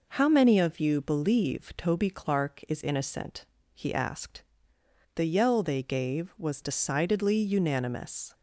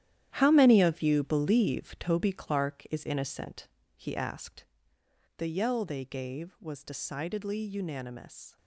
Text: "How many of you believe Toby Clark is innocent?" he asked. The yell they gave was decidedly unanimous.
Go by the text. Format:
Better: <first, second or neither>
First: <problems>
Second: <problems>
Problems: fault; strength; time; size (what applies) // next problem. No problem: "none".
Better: first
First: none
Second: gets quieter; strong; throughout; 11.5 dB